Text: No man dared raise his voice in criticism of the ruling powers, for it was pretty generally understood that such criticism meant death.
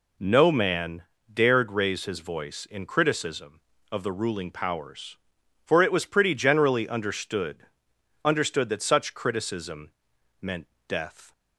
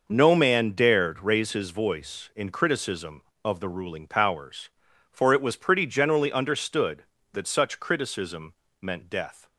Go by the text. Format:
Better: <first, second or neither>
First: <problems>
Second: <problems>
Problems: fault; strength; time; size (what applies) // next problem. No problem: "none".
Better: second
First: pauses between "man" and "dared"; slight; at 1.0 s; 0.28 s long // says "understood" twice; at 8.2 s // pauses between "criticism" and "meant"; noticeable; at 9.9 s; 0.50 s long // pauses between "meant" and "death"; slight; at 10.6 s; 0.22 s long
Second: pauses between "criticism" and "meant"; slight; at 8.5 s; 0.28 s long